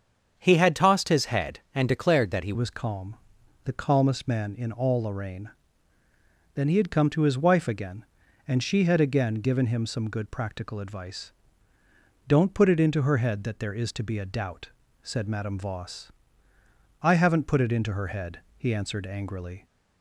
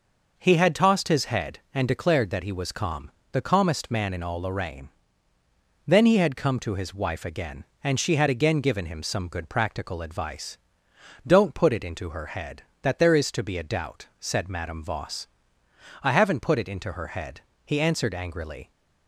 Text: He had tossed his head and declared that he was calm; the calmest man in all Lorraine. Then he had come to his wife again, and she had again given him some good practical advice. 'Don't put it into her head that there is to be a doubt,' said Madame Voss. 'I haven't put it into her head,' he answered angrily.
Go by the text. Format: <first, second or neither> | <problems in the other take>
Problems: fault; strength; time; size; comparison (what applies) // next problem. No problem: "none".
second | starts louder than the rest; strong; until 1.3 s; 7.5 dB // changes voice at "was"; from 2.5 s on; 17.1 s long